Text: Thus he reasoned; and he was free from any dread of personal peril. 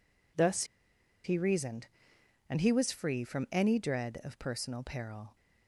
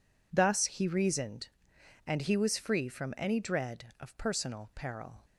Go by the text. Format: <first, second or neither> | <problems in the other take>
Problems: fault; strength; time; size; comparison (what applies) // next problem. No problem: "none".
second | pauses between "Thus" and "he"; noticeable; at 0.6 s; 0.60 s long